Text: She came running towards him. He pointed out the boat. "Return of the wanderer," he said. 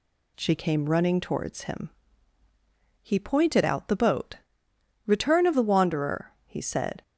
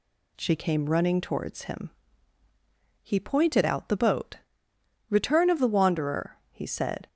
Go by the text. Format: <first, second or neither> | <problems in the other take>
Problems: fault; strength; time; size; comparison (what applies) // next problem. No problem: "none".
neither | none